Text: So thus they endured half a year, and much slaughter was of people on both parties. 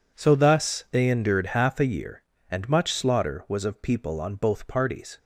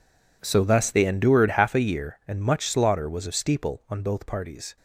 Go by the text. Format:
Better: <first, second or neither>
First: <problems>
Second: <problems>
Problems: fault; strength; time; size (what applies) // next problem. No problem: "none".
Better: first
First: none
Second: says "steeple" for "people"; at 3.3 s